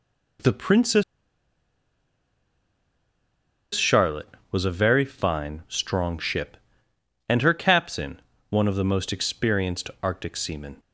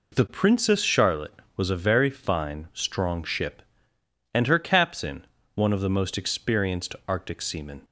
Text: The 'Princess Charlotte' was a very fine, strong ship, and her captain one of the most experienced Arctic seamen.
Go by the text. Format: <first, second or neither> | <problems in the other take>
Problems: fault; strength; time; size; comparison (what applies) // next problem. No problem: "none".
second | pauses between "Princess" and "Charlotte"; strong; at 1.0 s; 2.7 s long // pauses between "captain" and "one"; slight; at 8.2 s; 0.30 s long; slight in the second